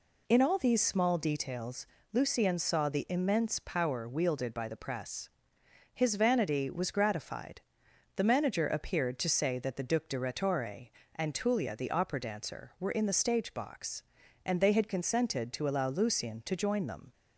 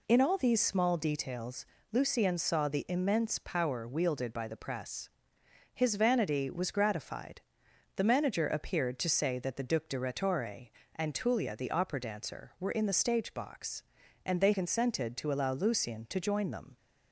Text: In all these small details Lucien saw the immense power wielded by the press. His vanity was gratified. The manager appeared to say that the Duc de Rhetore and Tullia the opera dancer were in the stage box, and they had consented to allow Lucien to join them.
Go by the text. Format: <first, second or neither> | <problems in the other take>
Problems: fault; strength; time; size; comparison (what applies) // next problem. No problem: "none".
first | pauses between "details" and "Lucien"; slight; at 1.6 s; 0.26 s long; slight in the first // skips "had"; at 14.5 s